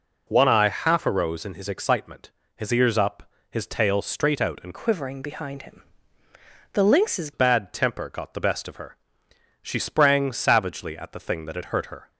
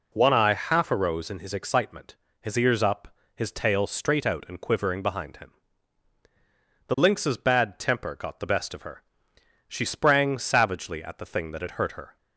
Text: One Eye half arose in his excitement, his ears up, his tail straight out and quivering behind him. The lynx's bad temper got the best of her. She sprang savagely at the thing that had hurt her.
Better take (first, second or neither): second